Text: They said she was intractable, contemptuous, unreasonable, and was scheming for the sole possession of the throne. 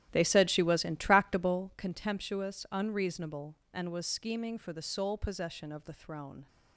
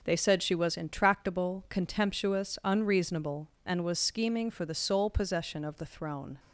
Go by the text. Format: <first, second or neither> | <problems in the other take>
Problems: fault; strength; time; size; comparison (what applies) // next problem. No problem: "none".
second | starts louder than the rest; strong; until 1.8 s; 11.5 dB